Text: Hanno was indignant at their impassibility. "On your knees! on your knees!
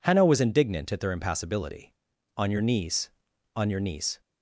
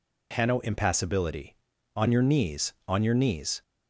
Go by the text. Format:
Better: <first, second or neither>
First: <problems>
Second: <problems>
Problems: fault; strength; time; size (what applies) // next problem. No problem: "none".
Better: first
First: none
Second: skips "was indignant at their"; at 0.5 s